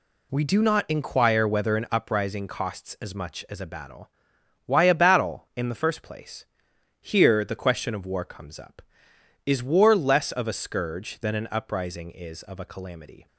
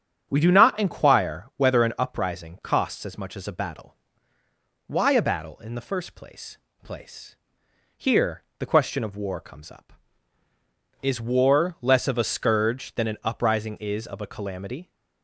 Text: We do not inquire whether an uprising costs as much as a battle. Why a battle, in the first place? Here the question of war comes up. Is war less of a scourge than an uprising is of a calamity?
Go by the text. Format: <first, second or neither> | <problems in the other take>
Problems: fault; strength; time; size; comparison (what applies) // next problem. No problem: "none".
first | starts louder than the rest; strong; until 1.3 s; 8 dB // says "place" twice; at 6.8 s // pauses between "Here" and "the"; slight; at 8.4 s; 0.18 s long